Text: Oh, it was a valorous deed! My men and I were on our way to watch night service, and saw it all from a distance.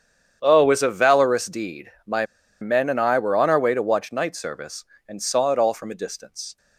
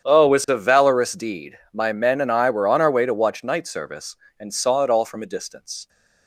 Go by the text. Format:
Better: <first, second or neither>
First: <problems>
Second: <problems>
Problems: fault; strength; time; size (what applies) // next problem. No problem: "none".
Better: second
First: starts louder than the rest; strong; until 1.4 s; 8.5 dB // pauses between "My" and "men"; slight; at 2.2 s; 0.35 s long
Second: starts louder than the rest; strong; until 1.0 s; 8.5 dB